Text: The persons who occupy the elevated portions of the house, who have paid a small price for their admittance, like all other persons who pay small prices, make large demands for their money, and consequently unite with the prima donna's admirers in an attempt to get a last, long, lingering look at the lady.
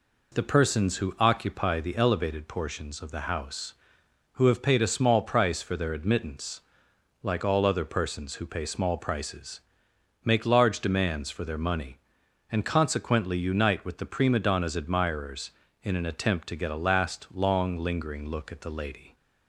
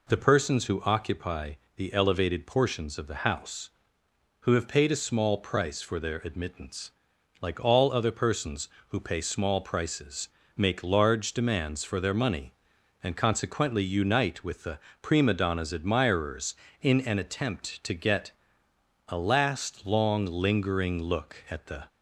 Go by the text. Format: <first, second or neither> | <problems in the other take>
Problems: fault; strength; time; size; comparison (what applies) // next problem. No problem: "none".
first | pauses between "occupy" and "the"; slight; at 1.5 s; 0.20 s long // pauses between "the" and "prima"; slight; at 14.7 s; 0.24 s long // pauses between "get" and "a"; noticeable; at 18.3 s; 0.78 s long // stops before "lady"; at 21.8 s